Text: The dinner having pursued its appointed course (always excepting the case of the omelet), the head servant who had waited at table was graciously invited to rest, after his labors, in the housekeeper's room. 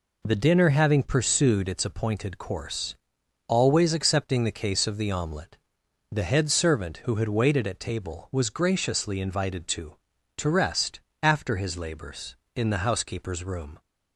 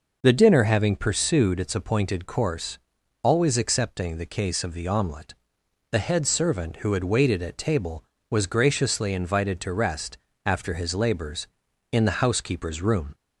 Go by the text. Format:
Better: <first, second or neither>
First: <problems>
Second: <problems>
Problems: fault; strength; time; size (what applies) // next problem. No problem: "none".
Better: second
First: says "to" twice; at 10.3 s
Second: none